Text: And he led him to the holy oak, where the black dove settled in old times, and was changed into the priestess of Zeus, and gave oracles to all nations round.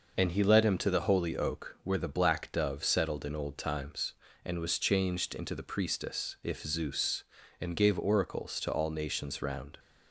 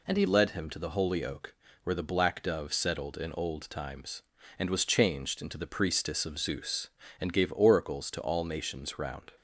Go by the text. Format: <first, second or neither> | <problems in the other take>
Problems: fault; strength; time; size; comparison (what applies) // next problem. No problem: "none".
second | says "if" for "of"; at 6.4 s